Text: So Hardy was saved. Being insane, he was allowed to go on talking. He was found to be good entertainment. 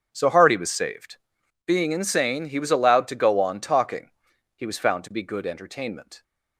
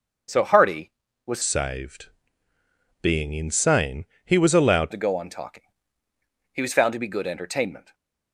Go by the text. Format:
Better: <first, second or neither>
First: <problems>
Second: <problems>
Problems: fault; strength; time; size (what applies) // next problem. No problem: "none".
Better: first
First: starts louder than the rest; until 1.1 s; 7 dB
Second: starts louder than the rest; until 1.6 s; 6.5 dB // changes voice from "saved" to "allowed"; from 1.4 to 4.9 s; 3.5 s long // stays silent after the last word; slight; from 7.8 s on; 0.5 s long